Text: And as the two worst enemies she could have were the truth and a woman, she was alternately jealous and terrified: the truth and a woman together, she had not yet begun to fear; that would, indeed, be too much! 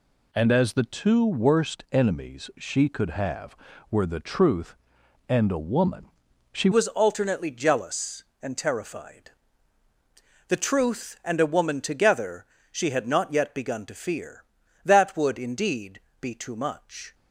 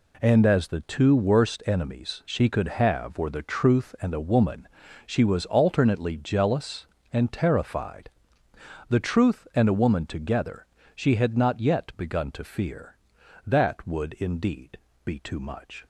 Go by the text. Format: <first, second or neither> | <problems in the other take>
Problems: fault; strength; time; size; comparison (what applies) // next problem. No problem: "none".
second | changes voice at "was"; from 6.7 s on; 10.4 s long